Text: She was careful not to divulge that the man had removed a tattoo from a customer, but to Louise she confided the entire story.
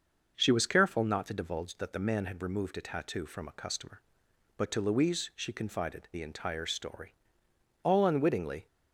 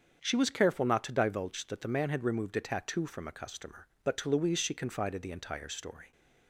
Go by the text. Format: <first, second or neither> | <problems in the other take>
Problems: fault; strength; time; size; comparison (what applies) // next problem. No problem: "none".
second | starts louder than the rest; noticeable; until 1.3 s; 6 dB; strong in the second // goes on to say "All unwittingly"; noticeable; from 7.8 s on; 0.82 s long